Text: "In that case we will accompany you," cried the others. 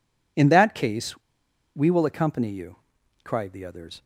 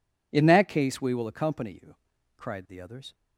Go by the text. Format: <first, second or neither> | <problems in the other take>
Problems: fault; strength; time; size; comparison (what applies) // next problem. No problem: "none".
second | pauses between "case" and "we"; noticeable; at 1.1 s; 0.60 s long